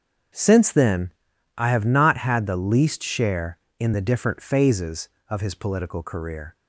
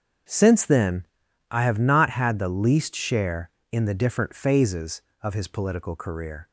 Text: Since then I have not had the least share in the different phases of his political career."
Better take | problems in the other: neither | starts louder than the rest; strong; the same in both // pauses between "then" and "I"; the same in both

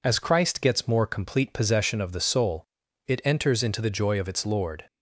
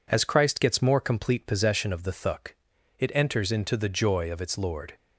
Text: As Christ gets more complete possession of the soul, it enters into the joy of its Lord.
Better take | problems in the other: first | says "thuk" for "soul"; at 2.1 s

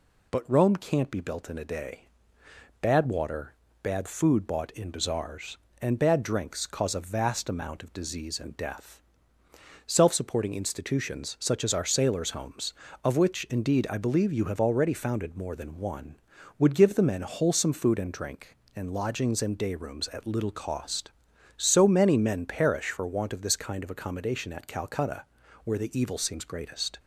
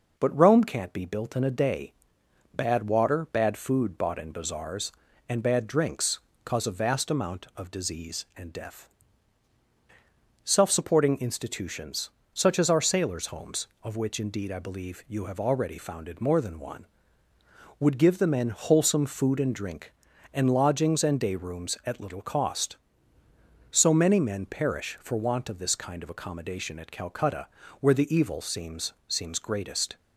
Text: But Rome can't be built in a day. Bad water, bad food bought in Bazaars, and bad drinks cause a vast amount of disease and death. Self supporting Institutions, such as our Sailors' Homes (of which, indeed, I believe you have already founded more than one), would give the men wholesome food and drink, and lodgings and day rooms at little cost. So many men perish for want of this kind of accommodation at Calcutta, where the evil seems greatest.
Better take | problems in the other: first | pauses between "drinks" and "cause"; slight; at 6.2 s; 0.24 s long // says "seems" twice; at 29.0 s

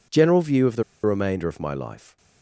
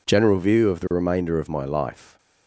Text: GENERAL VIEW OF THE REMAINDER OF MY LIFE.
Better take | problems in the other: second | pauses between "THE" and "REMAINDER"; slight; at 0.8 s; 0.21 s long

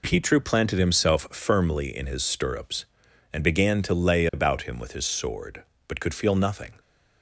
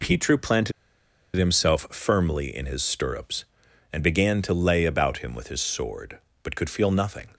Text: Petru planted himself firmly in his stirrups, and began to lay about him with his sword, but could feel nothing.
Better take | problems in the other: first | pauses between "planted" and "himself"; noticeable; at 0.7 s; 0.64 s long

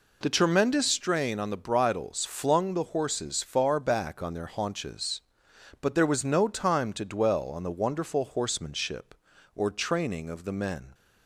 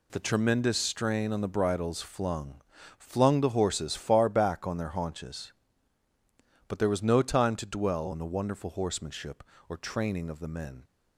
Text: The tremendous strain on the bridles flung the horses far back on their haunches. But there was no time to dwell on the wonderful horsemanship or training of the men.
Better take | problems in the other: first | says "flung" twice; at 2.9 s

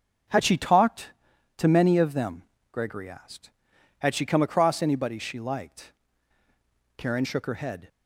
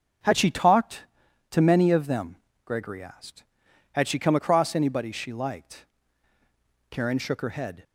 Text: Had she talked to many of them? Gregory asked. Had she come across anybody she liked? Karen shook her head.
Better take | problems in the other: neither | starts louder than the rest; the same in both

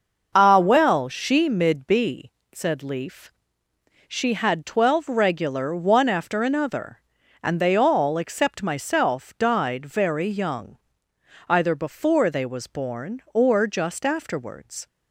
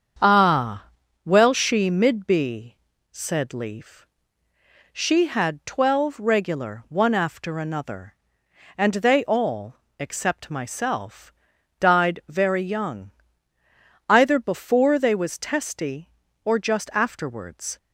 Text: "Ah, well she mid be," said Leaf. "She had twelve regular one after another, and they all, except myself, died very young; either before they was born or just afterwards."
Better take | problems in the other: first | starts louder than the rest; strong; until 1.6 s; 7.5 dB; noticeable in the first // says "testy" for "born"; at 15.3 s

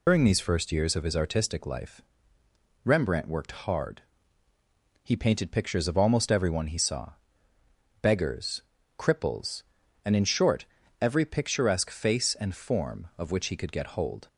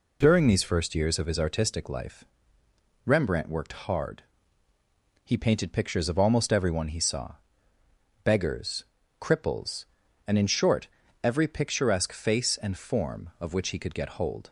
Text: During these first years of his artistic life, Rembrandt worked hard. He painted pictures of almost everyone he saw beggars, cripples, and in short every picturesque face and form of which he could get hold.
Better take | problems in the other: second | loses the start of "During"; at 0.0 s; 95 ms // pauses between "saw" and "beggars"; noticeable; at 7.1 s; 0.90 s long; noticeable in the second // pauses between "short" and "every"; slight; at 10.6 s; 0.36 s long; slight in the second

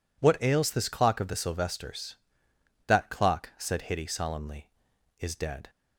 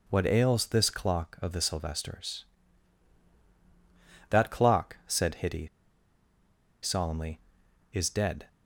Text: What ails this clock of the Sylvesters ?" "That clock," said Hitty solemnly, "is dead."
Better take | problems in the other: first | pauses between "Hitty" and "solemnly"; at 5.6 s; 1.1 s long

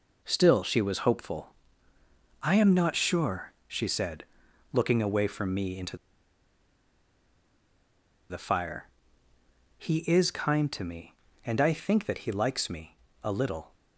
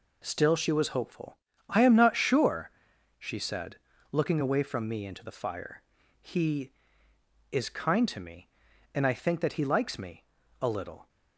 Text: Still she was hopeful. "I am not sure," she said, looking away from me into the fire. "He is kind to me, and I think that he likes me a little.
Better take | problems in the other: second | pauses between "into" and "the"; strong; at 5.9 s; 2.3 s long // pauses between "me" and "a"; slight; at 12.9 s; 0.26 s long; slight in the second

